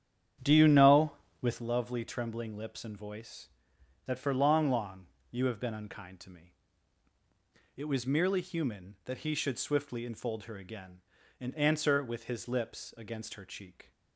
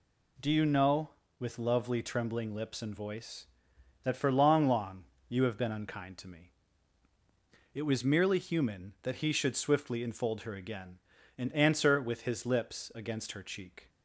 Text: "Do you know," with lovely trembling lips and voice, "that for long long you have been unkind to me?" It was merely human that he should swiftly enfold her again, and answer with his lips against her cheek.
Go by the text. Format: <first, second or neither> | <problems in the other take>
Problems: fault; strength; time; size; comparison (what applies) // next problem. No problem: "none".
second | starts louder than the rest; strong; until 1.6 s; 9 dB // pauses between "long" and "you"; slight; at 5.0 s; 0.24 s long; slight in the second